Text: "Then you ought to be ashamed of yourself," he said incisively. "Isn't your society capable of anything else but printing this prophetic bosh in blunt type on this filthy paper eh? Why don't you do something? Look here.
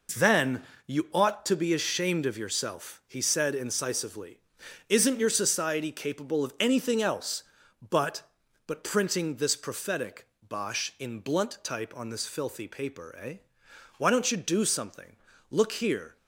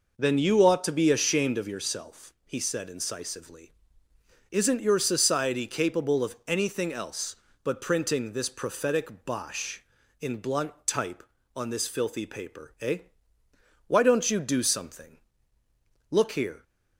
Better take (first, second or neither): second